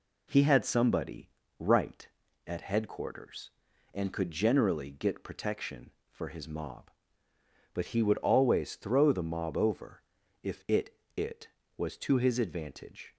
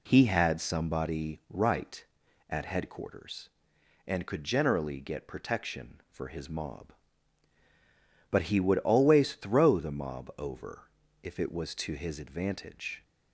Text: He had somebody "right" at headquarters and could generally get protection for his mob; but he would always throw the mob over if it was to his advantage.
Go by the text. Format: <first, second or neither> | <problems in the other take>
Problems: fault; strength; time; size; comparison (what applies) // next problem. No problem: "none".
second | pauses between "somebody" and "right"; slight; at 1.2 s; 0.28 s long // pauses between "over" and "if"; at 10.0 s; 0.42 s long; slight in the second // says "it" twice; at 11.1 s